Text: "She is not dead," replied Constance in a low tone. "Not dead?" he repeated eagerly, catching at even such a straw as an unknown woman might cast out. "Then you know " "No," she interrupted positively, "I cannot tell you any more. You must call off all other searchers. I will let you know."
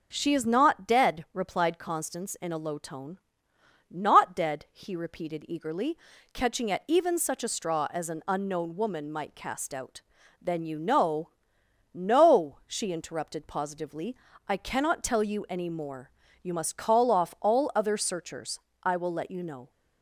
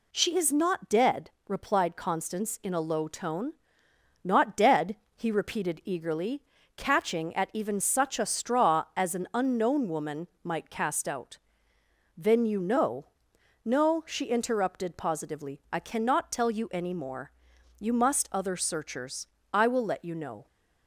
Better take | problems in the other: first | pauses between "woman" and "might"; slight; at 10.2 s; 0.16 s long // skips "call off all"; at 18.3 s

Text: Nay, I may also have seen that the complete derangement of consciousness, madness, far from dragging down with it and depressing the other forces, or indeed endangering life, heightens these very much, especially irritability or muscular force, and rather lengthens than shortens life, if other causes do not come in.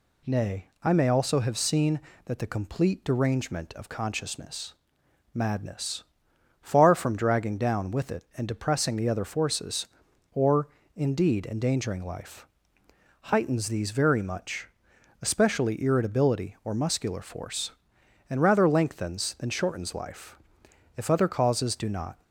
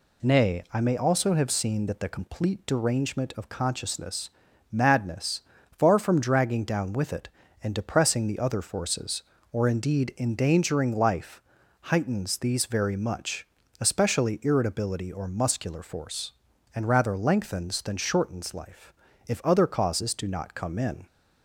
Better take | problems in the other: second | pauses between "or" and "indeed"; slight; at 10.6 s; 0.26 s long // stops before "come in"; at 22.2 s

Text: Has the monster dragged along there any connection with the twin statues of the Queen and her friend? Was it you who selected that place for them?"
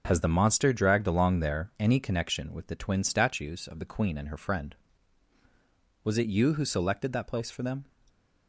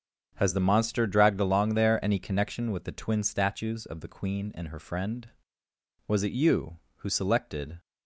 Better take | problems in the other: first | starts louder than the rest; strong; until 1.3 s; 7 dB // stops before "that place for them"; at 7.7 s

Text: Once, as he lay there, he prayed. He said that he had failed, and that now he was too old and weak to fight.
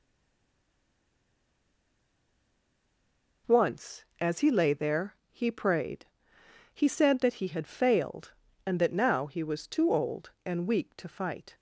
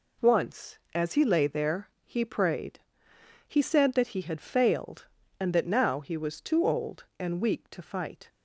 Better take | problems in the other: second | stays silent before the first word; strong; until 3.4 s; 3.4 s long

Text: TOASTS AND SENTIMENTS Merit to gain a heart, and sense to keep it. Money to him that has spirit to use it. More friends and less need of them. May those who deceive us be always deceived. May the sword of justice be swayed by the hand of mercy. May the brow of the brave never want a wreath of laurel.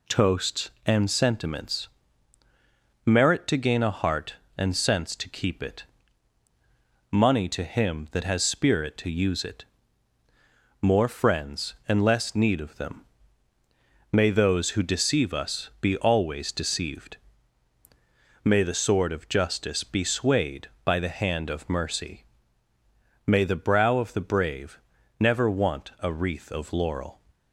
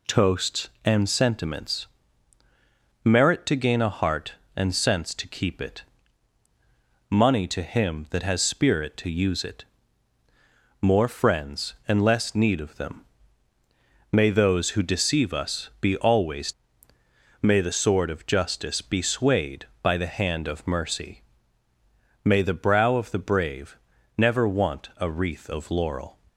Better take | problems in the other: first | pauses between "SENTIMENTS" and "Merit"; at 1.8 s; 1.1 s long; also in the first // skips "deceived"; at 16.9 s // pauses between "brave" and "never"; at 23.7 s; 0.40 s long; also in the first

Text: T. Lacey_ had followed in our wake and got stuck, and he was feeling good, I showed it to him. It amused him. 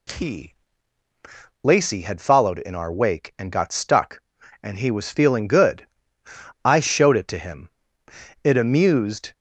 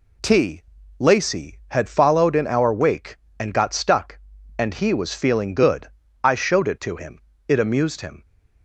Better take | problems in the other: second | stops before "him"; at 9.3 s

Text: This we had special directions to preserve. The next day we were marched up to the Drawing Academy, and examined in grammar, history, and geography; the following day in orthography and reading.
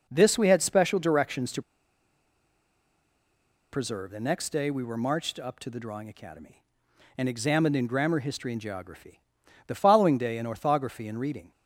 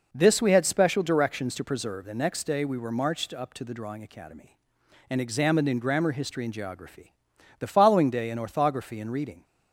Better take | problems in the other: second | pauses between "to" and "preserve"; strong; at 1.6 s; 2.1 s long

